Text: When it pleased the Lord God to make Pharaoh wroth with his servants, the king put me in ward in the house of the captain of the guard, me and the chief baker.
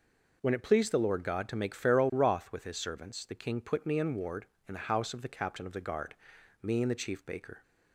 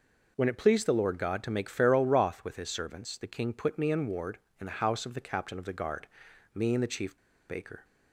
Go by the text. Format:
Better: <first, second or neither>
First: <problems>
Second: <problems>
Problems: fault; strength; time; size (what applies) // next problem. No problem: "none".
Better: first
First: none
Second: pauses between "chief" and "baker"; slight; at 7.1 s; 0.32 s long